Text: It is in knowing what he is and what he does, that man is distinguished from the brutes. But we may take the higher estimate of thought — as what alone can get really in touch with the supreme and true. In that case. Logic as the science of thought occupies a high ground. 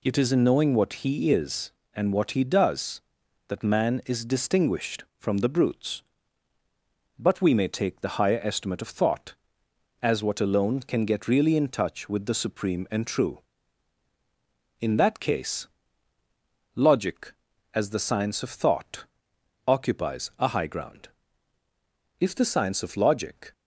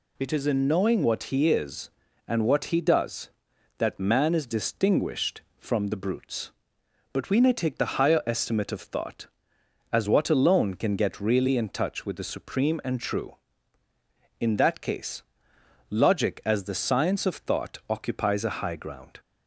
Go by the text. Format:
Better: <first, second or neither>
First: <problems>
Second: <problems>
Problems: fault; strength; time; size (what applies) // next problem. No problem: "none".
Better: second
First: pauses between "thought" and "occupies"; noticeable; at 19.0 s; 0.64 s long // goes on to say "If the science of Logic"; from 22.1 s on; 1.3 s long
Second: none